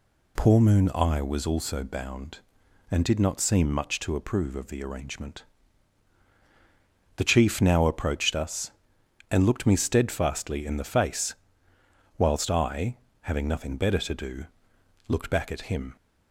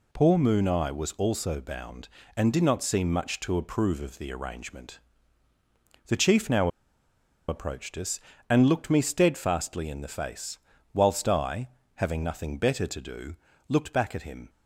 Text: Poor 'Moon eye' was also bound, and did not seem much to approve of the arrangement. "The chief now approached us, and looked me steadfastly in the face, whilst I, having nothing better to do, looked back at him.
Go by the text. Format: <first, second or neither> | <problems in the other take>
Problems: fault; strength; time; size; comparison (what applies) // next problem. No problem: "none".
first | pauses between "now" and "approached"; noticeable; at 6.6 s; 0.79 s long